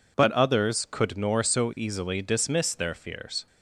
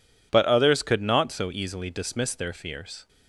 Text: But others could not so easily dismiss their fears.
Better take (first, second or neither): second